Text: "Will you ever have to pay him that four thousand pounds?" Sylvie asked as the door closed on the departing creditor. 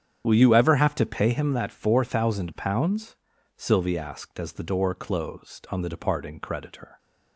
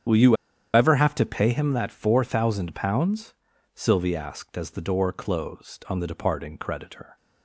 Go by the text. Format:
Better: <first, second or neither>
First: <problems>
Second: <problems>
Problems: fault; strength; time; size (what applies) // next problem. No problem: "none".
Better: first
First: starts louder than the rest; strong; until 1.2 s; 8.5 dB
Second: starts louder than the rest; strong; until 1.4 s; 8 dB // pauses between "you" and "ever"; at 0.3 s; 0.39 s long